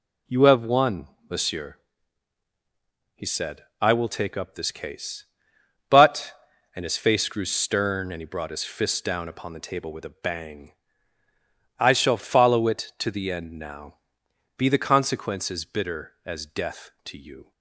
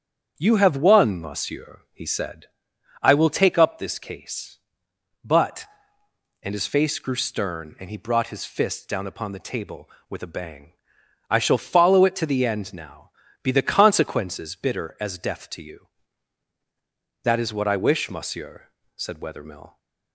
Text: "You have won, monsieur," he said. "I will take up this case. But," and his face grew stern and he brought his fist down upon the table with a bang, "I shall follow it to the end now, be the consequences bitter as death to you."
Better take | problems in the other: first | starts louder than the rest; strong; until 1.3 s; 8 dB // goes on to say "That is what I wish monsieur said Wethermill"; strong; from 17.2 s on; 2.5 s long

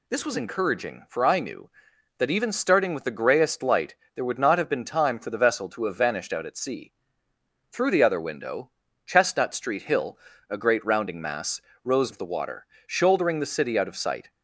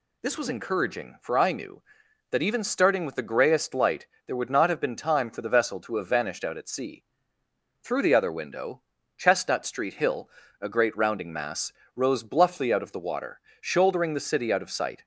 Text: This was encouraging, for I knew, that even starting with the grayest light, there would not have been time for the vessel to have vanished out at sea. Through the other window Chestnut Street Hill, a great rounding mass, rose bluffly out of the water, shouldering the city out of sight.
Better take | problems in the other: second | pauses between "window" and "Chestnut"; at 8.6 s; 0.38 s long; also in the second // skips "bluffly out"; at 12.1 s

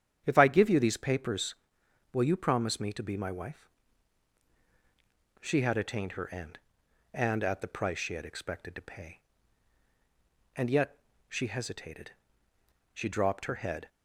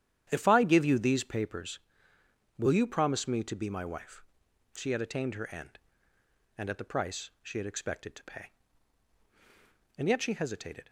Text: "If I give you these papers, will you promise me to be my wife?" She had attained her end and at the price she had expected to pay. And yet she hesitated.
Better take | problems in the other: second | starts louder than the rest; strong; until 1.2 s; 9 dB; strong in the second // pauses between "yet" and "she"; slight; at 10.9 s; 0.30 s long // goes on to say "She dropped her head"; noticeable; from 12.9 s on; 0.94 s long

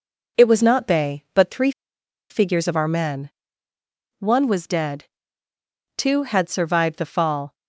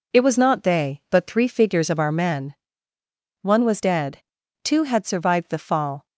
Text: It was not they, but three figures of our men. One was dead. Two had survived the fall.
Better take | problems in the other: second | pauses between "three" and "figures"; noticeable; at 1.7 s; 0.59 s long

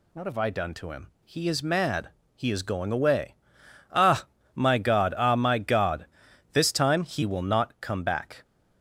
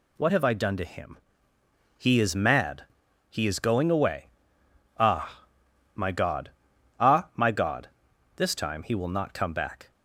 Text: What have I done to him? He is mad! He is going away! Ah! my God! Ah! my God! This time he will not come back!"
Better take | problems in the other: neither | none

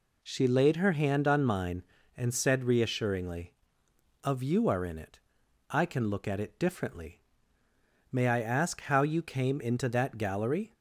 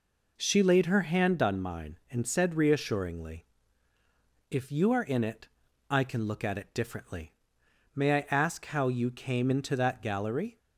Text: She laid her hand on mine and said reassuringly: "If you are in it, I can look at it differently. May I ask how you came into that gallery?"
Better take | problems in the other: second | says "Of" for "If"; at 4.2 s

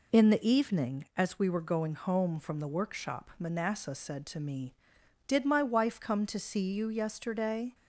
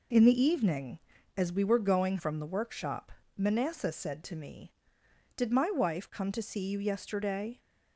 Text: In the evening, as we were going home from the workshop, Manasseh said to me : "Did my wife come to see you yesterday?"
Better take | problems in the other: first | skips "home"; at 2.1 s

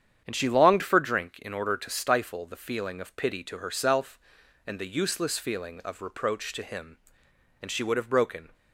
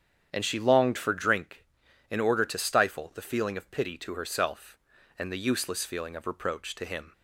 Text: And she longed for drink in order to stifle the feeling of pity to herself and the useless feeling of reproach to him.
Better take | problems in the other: second | starts louder than the rest; strong; until 1.2 s; 8.5 dB; strong in the second // goes on to say "And she would have broken"; noticeable; from 7.6 s on; 0.92 s long

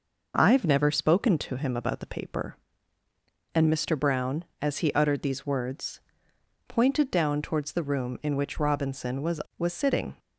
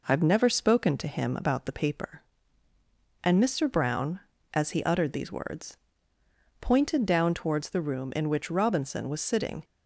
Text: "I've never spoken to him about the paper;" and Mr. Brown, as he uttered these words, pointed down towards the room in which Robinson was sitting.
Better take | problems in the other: second | says "was" twice; at 9.5 s

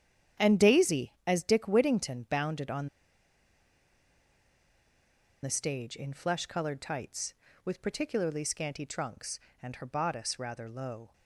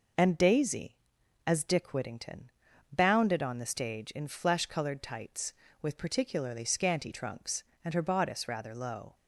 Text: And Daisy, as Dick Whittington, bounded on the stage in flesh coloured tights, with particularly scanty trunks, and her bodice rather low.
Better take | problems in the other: second | starts louder than the rest; strong; until 1.5 s; 9 dB // pauses between "on" and "the"; strong; at 2.8 s; 2.5 s long

